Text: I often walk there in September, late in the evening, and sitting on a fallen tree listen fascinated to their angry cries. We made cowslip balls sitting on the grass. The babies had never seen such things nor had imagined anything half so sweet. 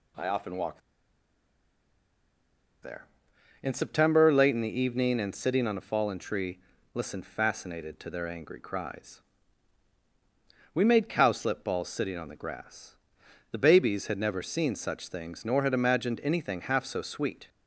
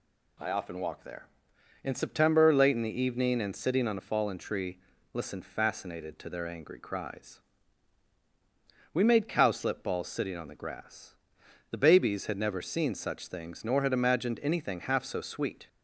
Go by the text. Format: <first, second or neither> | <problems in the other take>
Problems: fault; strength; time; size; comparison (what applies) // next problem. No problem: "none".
second | pauses between "walk" and "there"; strong; at 0.8 s; 2.0 s long // pauses between "tree" and "listen"; slight; at 6.5 s; 0.36 s long; slight in the second